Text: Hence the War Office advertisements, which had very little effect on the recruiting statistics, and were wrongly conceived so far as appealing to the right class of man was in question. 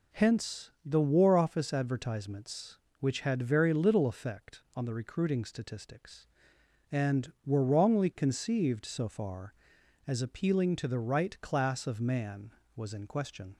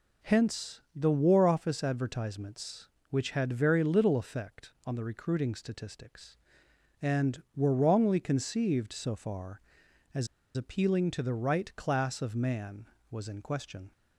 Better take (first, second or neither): first